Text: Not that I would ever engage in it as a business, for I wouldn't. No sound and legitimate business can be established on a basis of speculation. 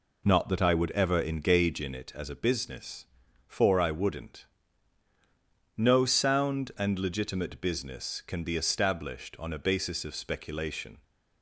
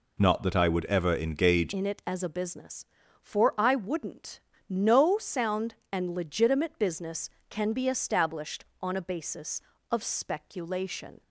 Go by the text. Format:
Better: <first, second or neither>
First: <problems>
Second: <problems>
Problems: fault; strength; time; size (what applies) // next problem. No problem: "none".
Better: first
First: none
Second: changes voice at "in"; from 1.7 s on; 9.5 s long